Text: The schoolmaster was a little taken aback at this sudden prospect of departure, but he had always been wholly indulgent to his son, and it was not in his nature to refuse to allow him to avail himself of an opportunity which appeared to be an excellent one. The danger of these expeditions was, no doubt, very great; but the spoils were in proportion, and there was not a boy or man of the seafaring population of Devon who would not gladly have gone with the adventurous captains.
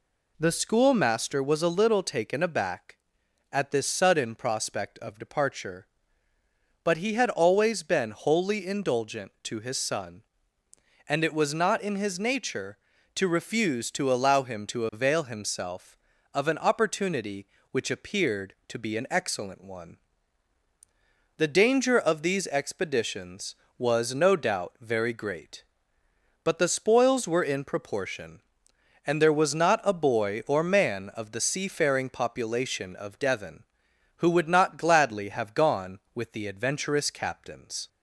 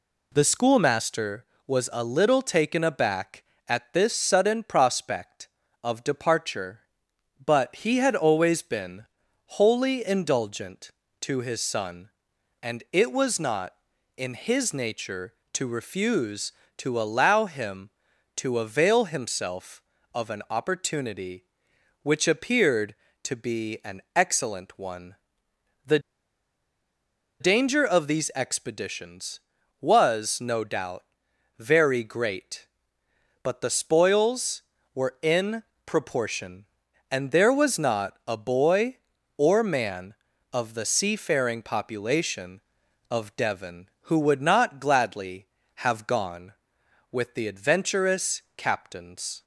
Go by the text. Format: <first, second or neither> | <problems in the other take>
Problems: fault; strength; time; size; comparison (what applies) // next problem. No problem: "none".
first | pauses between "been" and "wholly"; at 9.0 s; 0.40 s long // pauses between "The" and "danger"; strong; at 25.9 s; 1.4 s long // pauses between "in" and "proportion"; slight; at 35.6 s; 0.24 s long